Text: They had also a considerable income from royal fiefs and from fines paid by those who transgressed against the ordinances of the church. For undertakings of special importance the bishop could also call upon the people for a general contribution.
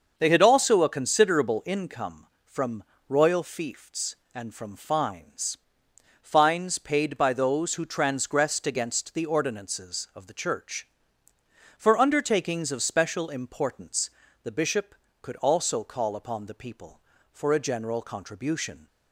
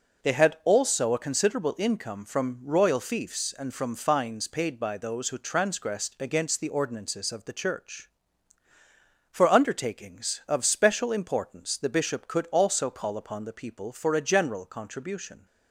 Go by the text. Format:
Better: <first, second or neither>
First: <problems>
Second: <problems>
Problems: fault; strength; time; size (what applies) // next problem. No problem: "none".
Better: second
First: starts louder than the rest; until 1.1 s; 6 dB // pauses between "from" and "royal"; slight; at 2.8 s; 0.24 s long // says "fines" twice; at 6.2 s // pauses between "importance" and "the"; slight; at 14.0 s; 0.34 s long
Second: none